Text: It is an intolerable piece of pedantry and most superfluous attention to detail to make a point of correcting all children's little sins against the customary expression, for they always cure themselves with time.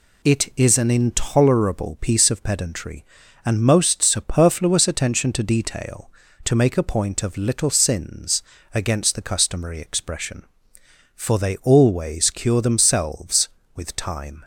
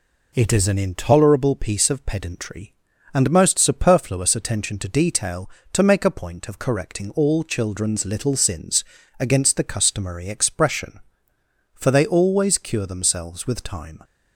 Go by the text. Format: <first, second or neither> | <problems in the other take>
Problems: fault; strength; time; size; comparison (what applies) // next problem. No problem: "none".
second | skips "correcting all children's"; at 7.3 s // pauses between "sins" and "against"; slight; at 8.4 s; 0.32 s long; slight in the second